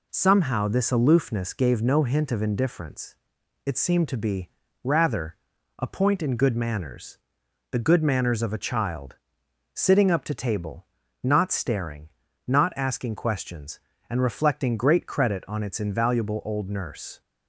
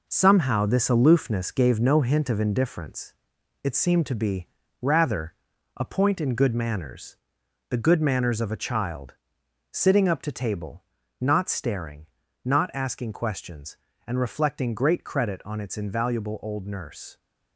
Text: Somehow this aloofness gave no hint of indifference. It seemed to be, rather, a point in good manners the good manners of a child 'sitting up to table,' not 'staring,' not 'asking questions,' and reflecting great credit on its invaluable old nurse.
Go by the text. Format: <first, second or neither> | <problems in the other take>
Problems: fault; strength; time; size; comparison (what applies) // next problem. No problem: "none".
first | gets quieter; throughout; 6.5 dB // pauses between "manners" and "the"; noticeable; at 7.1 s; 0.52 s long; noticeable in the first // pauses between "child" and "sitting"; noticeable; at 9.1 s; 0.56 s long; noticeable in the first